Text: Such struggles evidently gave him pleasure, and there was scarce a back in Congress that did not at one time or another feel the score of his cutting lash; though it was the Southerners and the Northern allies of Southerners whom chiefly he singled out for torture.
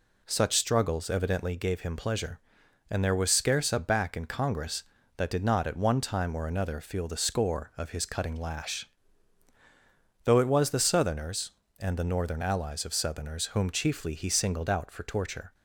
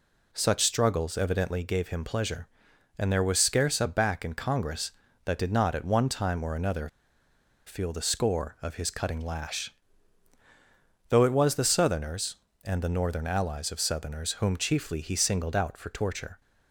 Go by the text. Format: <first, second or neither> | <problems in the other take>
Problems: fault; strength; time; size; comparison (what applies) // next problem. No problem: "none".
first | pauses between "another" and "feel"; noticeable; at 6.8 s; 0.78 s long